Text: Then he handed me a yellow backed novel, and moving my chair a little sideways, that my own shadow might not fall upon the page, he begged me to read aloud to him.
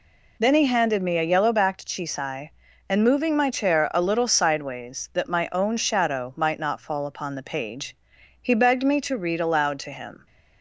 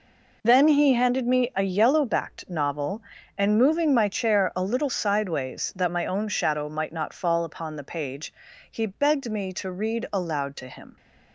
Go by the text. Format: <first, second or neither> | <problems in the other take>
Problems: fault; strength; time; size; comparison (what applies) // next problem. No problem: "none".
second | says "chisai" for "novel"; at 1.8 s